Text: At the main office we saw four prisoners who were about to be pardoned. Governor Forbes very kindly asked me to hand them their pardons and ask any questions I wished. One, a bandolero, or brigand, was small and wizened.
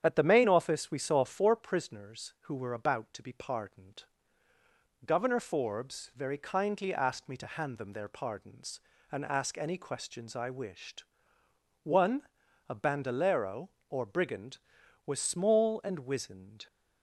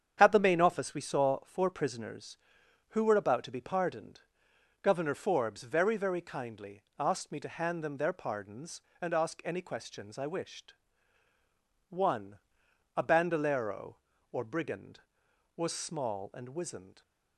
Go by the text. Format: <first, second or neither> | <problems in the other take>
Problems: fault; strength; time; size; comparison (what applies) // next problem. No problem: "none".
first | starts louder than the rest; strong; until 1.2 s; 8 dB; strong in the first // says "very" twice; at 5.9 s // pauses between "kindly" and "asked"; slight; at 6.8 s; 0.18 s long